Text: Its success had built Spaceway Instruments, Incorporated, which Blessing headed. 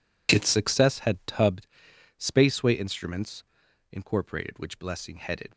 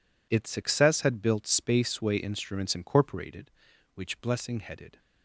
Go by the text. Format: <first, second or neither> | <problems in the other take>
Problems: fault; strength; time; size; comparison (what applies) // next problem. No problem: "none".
second | says "tubbed" for "built"; at 1.2 s